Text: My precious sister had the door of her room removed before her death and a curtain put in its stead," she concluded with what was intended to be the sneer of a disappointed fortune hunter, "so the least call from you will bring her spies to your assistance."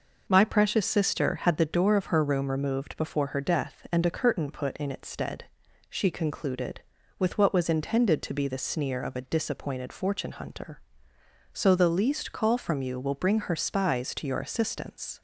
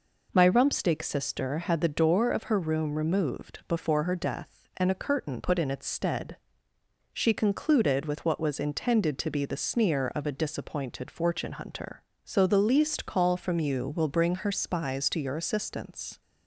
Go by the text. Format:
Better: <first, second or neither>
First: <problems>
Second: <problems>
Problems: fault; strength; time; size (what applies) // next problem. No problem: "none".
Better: first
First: none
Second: says "rumpsteak" for "precious"; at 0.4 s